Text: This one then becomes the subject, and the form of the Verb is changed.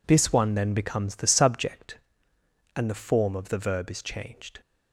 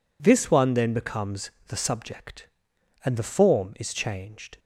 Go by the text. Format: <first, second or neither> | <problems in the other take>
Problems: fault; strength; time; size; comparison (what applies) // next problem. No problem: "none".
first | pauses between "becomes" and "the"; slight; at 1.4 s; 0.20 s long // skips "of the Verb"; at 3.7 s